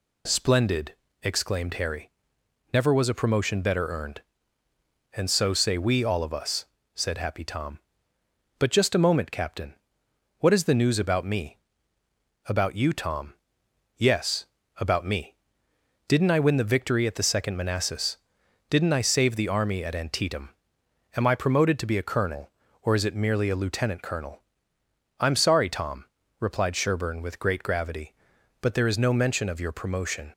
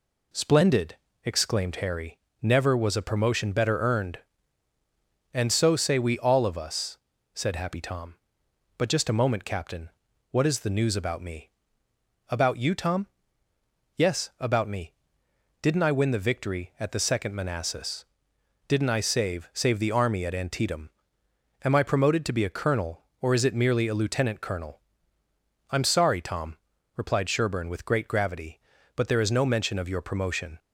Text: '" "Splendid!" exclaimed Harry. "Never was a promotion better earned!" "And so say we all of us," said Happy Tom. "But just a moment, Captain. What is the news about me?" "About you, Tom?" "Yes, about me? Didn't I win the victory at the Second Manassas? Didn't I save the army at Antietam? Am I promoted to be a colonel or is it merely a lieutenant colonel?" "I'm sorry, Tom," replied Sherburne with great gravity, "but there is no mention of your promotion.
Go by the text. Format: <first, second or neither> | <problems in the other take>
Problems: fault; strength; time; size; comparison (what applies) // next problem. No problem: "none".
first | says "save" twice; at 19.5 s